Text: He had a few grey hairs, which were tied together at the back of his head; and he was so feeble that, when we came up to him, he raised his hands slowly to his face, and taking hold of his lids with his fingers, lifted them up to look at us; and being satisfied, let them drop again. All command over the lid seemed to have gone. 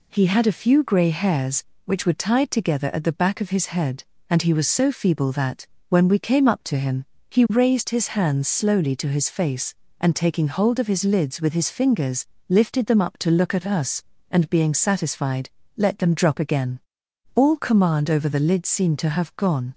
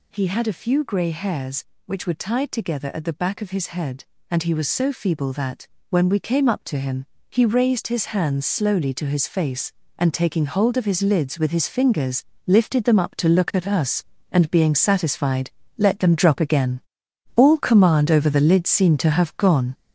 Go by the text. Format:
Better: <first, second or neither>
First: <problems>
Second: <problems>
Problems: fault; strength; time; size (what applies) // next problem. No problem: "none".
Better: first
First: none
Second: gets louder; throughout; 6 dB